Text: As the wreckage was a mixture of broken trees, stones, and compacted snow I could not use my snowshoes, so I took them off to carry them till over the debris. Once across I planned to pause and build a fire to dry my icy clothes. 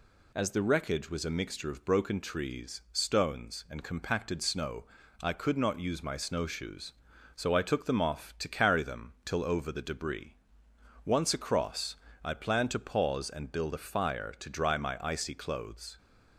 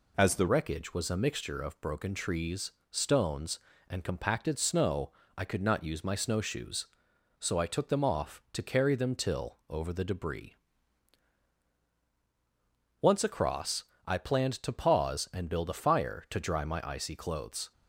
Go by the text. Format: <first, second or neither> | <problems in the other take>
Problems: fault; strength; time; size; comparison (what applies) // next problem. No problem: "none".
first | changes voice at "wreckage"; from 0.4 s on; 17.3 s long // pauses between "snow" and "I"; slight; at 5.1 s; 0.26 s long; slight in the first // pauses between "across" and "I"; slight; at 13.8 s; 0.20 s long; slight in the first